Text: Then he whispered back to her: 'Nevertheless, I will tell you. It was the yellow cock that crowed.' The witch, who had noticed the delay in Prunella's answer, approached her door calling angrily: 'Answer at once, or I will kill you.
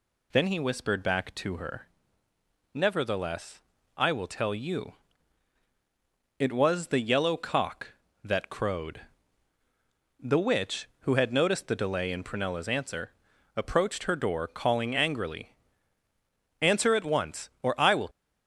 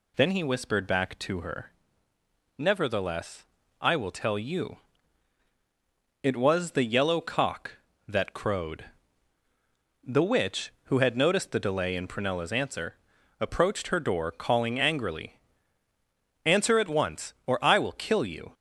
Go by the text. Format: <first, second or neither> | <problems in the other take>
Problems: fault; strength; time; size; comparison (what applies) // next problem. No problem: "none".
second | stops before "kill you"; at 18.1 s